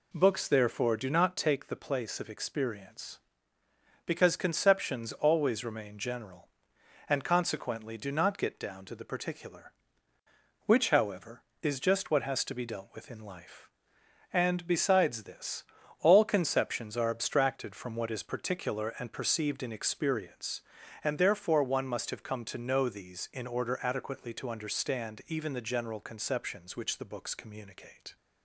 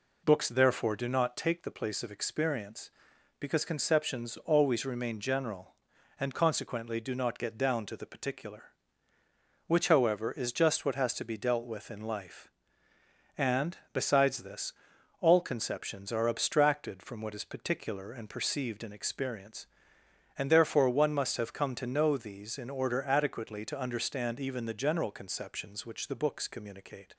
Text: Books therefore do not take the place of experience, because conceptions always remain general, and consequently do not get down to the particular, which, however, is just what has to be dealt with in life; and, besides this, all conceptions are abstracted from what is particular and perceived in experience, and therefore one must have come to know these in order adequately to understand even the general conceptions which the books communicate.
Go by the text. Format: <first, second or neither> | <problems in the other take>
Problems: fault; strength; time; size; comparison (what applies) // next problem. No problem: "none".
neither | none